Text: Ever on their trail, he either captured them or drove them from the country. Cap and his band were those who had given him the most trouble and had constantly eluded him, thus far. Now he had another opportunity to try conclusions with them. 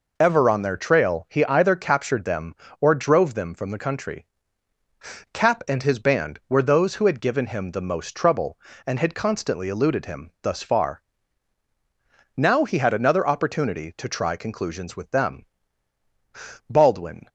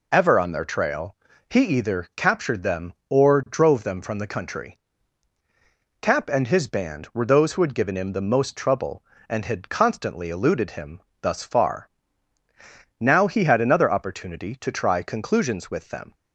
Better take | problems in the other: second | goes on to say "Baldwin"; from 16.6 s on; 0.56 s long

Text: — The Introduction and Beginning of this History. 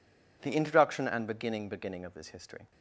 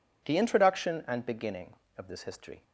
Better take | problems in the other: second | says "Beginning" twice; at 1.6 s

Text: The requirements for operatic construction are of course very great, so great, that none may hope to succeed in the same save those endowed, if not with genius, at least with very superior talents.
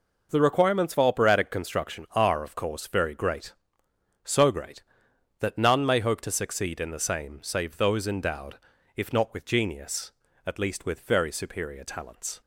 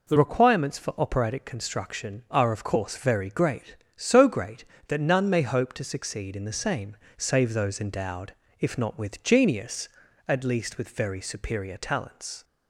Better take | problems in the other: first | changes voice at "requirements"; from 0.1 s on; 12.3 s long // pauses between "same" and "save"; slight; at 6.9 s; 0.22 s long

